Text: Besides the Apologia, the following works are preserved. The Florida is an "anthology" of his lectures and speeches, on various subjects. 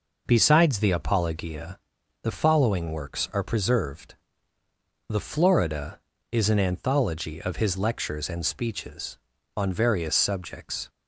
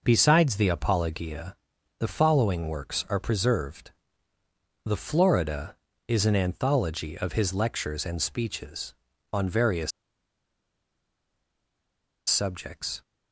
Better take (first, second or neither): first